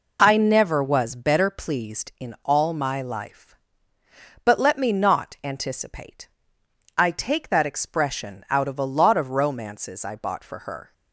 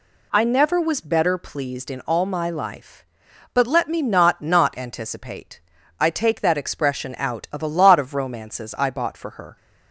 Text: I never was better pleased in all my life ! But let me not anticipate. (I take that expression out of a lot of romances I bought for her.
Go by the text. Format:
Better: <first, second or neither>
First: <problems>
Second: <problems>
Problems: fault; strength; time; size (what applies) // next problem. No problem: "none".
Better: first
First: none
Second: says "not" twice; at 4.4 s